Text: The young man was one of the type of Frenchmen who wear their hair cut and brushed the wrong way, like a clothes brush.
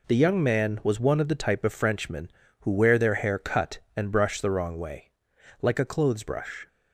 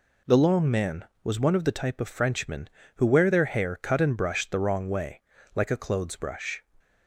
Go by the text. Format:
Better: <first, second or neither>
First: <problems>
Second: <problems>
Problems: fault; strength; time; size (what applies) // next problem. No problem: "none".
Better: first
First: none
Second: says "long" for "young"; at 0.3 s